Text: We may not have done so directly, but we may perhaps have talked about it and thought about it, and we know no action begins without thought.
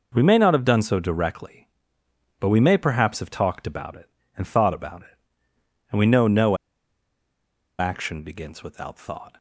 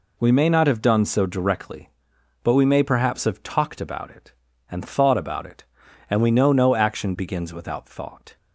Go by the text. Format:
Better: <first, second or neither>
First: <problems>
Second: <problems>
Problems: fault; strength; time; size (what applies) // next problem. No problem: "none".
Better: second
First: pauses between "no" and "action"; at 6.5 s; 1.2 s long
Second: none